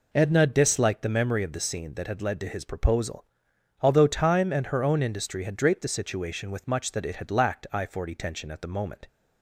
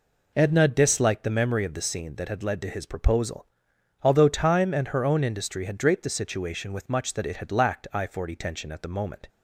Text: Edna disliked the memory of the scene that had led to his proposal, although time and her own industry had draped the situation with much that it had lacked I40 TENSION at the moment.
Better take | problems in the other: neither | none

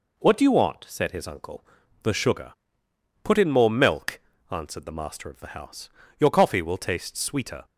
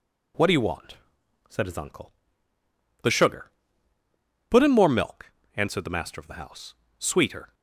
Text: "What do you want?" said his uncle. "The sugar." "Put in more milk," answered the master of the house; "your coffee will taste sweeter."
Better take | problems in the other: first | skips "your coffee will taste"; at 6.8 s

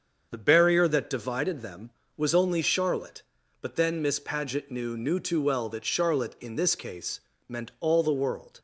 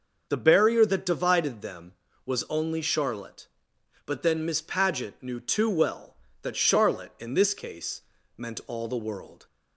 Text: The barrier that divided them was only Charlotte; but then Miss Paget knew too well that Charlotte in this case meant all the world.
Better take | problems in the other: second | starts louder than the rest; until 1.3 s; 7 dB // says "knew" twice; at 4.9 s // pauses between "case" and "meant"; slight; at 7.1 s; 0.28 s long; slight in the second

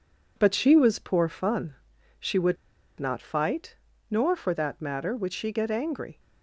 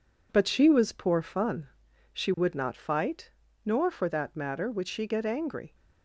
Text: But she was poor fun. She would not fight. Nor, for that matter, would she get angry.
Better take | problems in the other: second | pauses between "would" and "not"; at 2.5 s; 0.43 s long

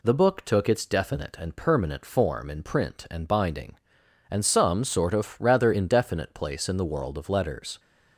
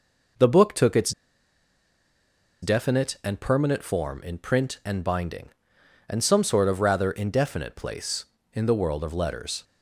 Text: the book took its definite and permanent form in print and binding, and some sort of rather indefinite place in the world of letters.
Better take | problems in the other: first | pauses between "its" and "definite"; strong; at 1.1 s; 1.5 s long

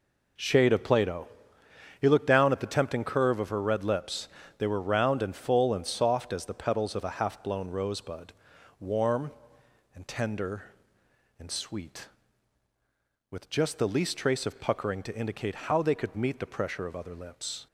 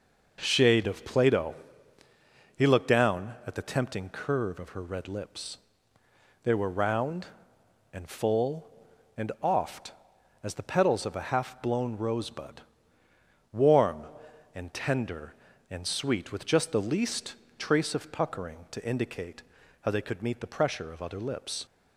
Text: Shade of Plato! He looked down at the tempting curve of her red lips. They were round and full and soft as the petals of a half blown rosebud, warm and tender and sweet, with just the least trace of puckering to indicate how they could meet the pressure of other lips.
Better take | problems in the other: first | says "oft" for "soft"; at 9.4 s // pauses between "least" and "trace"; slight; at 17.3 s; 0.22 s long // pauses between "indicate" and "how"; at 19.4 s; 0.40 s long

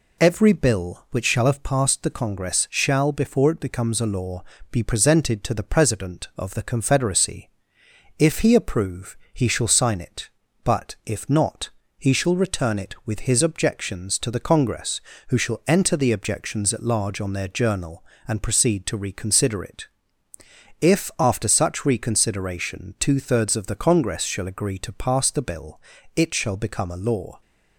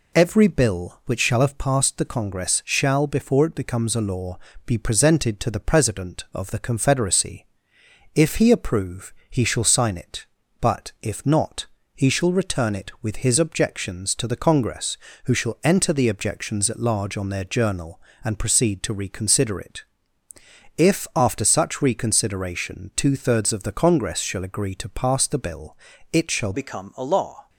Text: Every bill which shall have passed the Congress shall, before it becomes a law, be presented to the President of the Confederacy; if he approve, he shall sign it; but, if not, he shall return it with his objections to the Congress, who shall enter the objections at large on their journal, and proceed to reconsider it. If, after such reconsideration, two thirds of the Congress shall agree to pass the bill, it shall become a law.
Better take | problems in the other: first | changes voice at "become"; from 26.5 s on; 0.9 s long

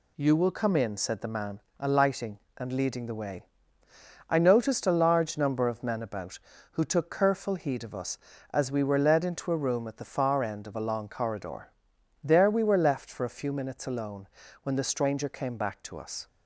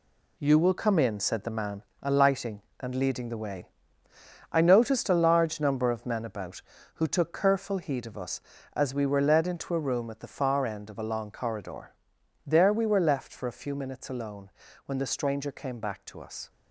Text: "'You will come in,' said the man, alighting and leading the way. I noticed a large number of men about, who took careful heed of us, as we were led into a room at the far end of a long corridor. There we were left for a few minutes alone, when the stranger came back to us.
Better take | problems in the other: first | gets quieter; strong; throughout; 7.5 dB

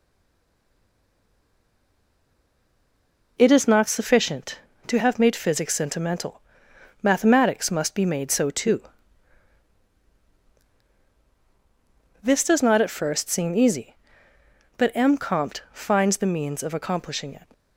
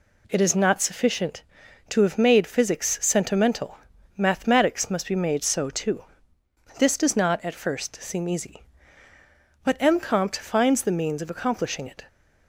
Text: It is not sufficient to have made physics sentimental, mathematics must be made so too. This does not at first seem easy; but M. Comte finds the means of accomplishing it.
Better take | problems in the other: second | stays silent before the first word; strong; until 3.3 s; 3.3 s long

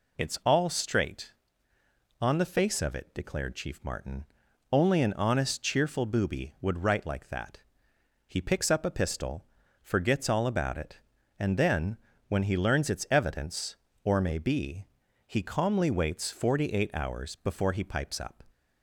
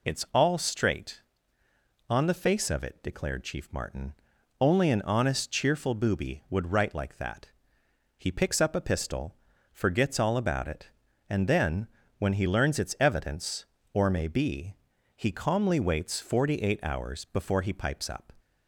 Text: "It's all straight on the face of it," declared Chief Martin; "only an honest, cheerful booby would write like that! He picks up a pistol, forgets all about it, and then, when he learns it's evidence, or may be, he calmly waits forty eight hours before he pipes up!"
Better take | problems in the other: neither | none

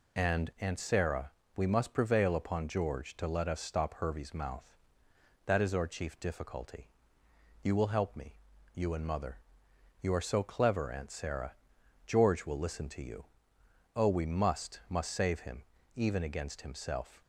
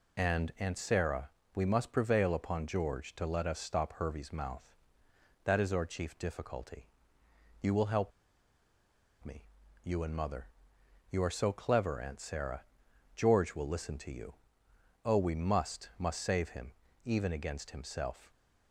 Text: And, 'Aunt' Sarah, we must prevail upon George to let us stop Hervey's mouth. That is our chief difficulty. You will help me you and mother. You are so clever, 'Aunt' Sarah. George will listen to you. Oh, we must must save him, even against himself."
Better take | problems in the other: first | pauses between "help" and "me"; at 8.1 s; 1.1 s long // pauses between "me" and "you"; at 9.4 s; 0.38 s long; also in the first

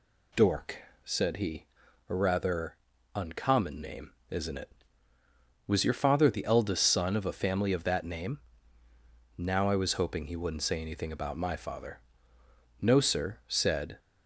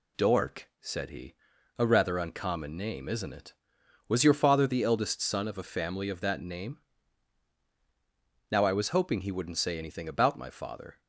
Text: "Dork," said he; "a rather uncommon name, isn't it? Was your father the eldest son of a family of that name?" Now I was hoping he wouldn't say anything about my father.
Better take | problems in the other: second | pauses between "rather" and "uncommon"; at 2.7 s; 0.38 s long // goes on to say "No sir said"; noticeable; from 12.8 s on; 1.1 s long

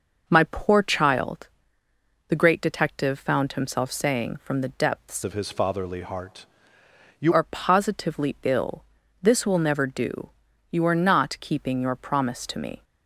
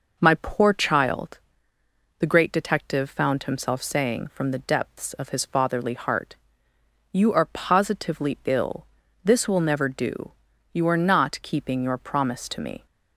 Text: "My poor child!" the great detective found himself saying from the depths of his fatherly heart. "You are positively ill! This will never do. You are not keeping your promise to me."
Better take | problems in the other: second | changes voice from "of" to "You"; from 5.2 to 7.3 s; 2.1 s long

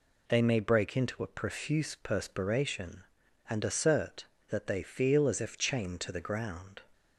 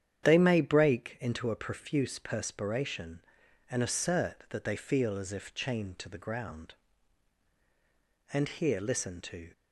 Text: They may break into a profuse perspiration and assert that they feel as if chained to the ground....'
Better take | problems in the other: first | starts louder than the rest; strong; until 1.2 s; 9 dB // goes on to say "And here listen to"; noticeable; from 8.3 s on; 1.1 s long

